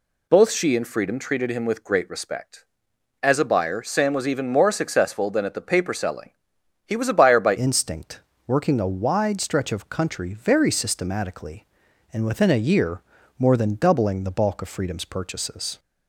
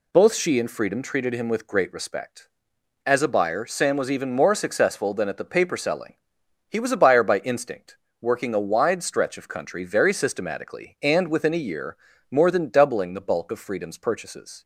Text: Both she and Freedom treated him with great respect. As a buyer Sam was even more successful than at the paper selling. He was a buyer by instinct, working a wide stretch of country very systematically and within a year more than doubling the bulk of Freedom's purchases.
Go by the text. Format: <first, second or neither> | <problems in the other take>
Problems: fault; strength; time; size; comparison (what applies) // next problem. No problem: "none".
second | changes voice at "instinct"; from 7.5 s on; 8.2 s long // pauses between "year" and "more"; at 13.0 s; 0.38 s long; slight in the second